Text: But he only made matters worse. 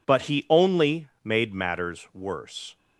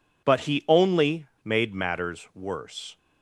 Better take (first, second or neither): neither